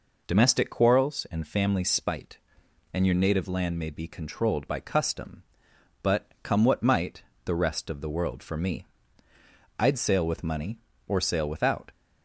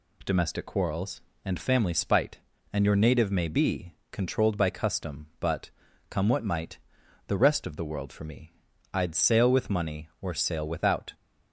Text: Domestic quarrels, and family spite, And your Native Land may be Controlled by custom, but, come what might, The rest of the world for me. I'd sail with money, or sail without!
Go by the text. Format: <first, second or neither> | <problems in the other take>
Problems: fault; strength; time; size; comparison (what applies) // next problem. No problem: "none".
first | skips "Land"; at 3.3 s // pauses between "be" and "Controlled"; slight; at 3.9 s; 0.18 s long